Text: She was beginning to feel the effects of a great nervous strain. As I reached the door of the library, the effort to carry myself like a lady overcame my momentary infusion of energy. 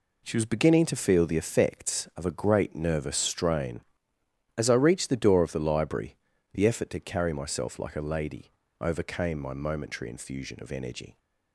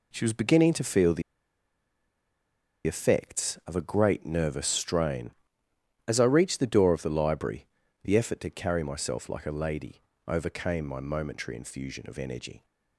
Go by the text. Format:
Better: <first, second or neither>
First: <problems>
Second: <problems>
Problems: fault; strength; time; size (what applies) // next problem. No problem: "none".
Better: first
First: pauses between "lady" and "overcame"; slight; at 8.5 s; 0.27 s long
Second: pauses between "the" and "effects"; strong; at 1.2 s; 1.6 s long // pauses between "lady" and "overcame"; slight; at 10.0 s; 0.24 s long